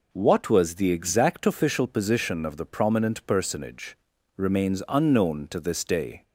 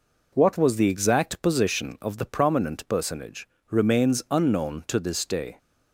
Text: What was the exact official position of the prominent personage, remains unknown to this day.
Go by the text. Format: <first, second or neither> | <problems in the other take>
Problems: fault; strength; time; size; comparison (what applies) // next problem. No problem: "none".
first | skips "official"; at 1.4 s